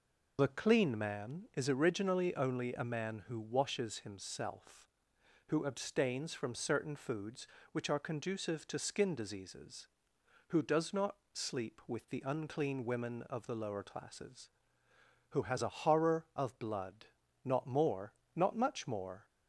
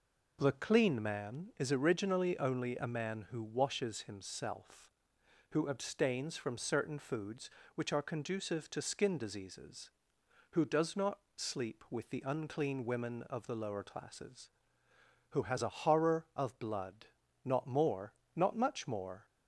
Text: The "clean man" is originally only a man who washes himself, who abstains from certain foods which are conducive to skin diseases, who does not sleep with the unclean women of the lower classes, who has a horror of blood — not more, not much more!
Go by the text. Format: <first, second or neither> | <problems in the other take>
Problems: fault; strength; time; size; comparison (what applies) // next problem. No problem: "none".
second | loses the start of "The"; at 0.3 s; 45 ms // pauses between "not" and "sleep"; slight; at 11.1 s; 0.16 s long; slight in the second